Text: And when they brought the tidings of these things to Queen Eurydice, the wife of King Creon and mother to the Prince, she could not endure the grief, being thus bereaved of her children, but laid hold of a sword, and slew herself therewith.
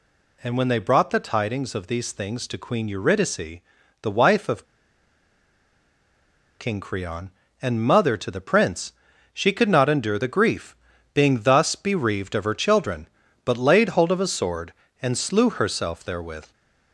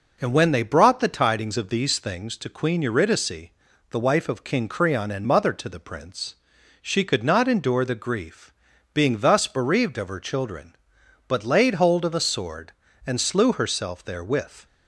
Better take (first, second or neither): second